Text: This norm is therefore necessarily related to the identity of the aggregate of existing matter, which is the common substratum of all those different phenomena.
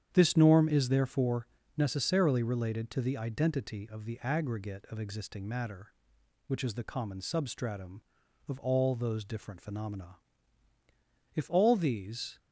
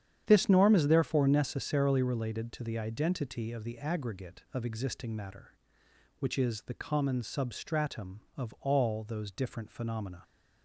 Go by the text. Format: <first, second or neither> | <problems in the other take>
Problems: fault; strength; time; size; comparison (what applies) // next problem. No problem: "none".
second | starts louder than the rest; strong; until 1.1 s; 9 dB; strong in the second // pauses between "therefore" and "necessarily"; slight; at 1.4 s; 0.30 s long // goes on to say "If all these"; noticeable; from 11.3 s on; 1.0 s long